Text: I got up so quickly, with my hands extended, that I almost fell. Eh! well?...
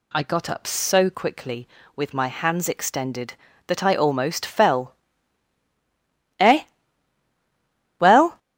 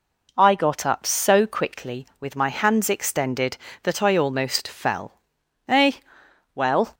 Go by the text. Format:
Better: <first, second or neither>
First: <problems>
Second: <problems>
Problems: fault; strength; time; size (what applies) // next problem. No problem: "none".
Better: second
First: gets louder; strong; throughout; 8.5 dB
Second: none